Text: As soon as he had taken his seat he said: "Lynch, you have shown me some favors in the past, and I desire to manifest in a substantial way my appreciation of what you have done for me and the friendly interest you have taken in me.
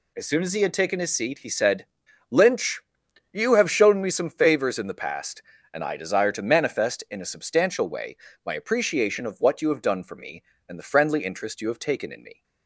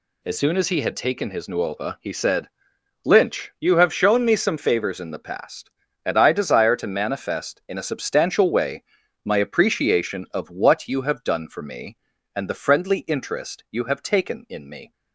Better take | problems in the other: first | says "nuova" for "seat"; at 1.4 s // pauses between "way" and "my"; at 8.8 s; 0.40 s long; slight in the first

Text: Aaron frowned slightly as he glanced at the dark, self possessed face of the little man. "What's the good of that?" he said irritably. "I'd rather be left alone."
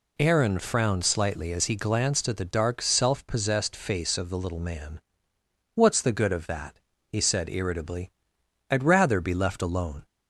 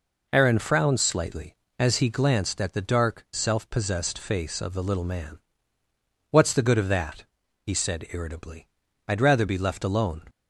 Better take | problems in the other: neither | none

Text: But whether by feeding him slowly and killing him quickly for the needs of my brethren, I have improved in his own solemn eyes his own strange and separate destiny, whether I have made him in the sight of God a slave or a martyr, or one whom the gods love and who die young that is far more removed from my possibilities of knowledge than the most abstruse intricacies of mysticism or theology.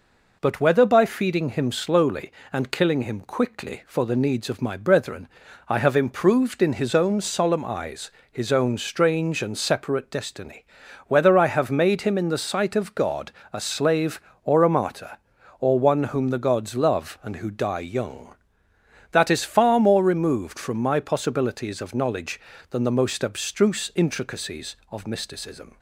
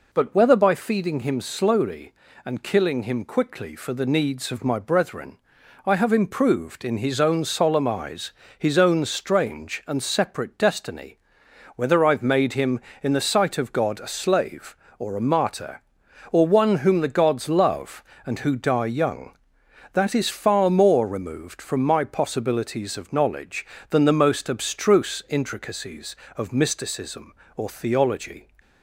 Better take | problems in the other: second | pauses between "eyes" and "his"; slight; at 8.0 s; 0.22 s long; slight in the second // pauses between "God" and "a"; slight; at 13.3 s; 0.20 s long // stops before "or theology"; at 25.7 s

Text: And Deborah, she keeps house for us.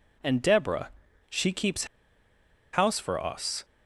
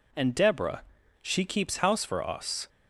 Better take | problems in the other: second | pauses between "keeps" and "house"; noticeable; at 1.8 s; 0.87 s long

